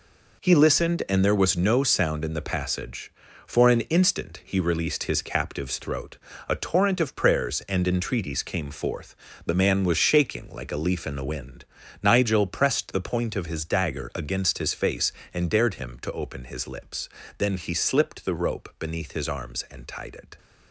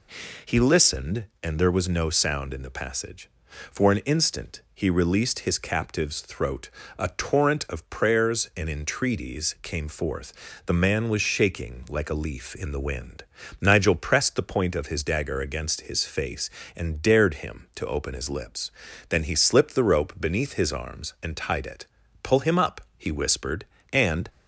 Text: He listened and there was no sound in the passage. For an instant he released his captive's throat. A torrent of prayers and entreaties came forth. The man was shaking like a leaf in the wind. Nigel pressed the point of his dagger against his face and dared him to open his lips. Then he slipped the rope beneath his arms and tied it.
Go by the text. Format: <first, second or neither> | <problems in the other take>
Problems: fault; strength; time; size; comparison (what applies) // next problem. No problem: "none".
first | goes on to say "Pull him up he whispered and"; strong; from 22.2 s on; 2.0 s long